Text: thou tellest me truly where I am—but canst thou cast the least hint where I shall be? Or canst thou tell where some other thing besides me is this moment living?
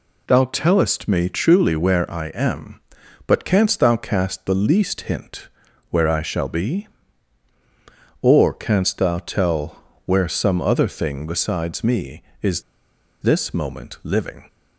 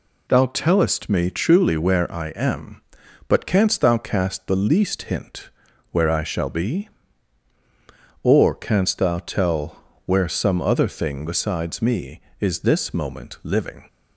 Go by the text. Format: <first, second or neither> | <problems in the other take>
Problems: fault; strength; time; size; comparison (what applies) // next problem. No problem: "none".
second | pauses between "hint" and "where"; at 5.4 s; 0.42 s long; also in the second // pauses between "tell" and "where"; slight; at 9.8 s; 0.22 s long; slight in the second // pauses between "is" and "this"; noticeable; at 12.6 s; 0.60 s long